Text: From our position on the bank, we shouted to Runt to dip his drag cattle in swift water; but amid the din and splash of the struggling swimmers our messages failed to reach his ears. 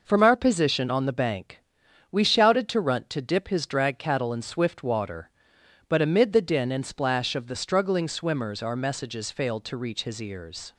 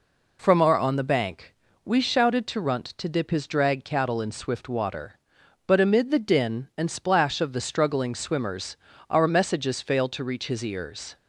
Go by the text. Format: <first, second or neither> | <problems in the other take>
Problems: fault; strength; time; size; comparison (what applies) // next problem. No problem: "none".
first | skips "position"; at 0.7 s // pauses between "swimmers" and "our"; slight; at 8.7 s; 0.32 s long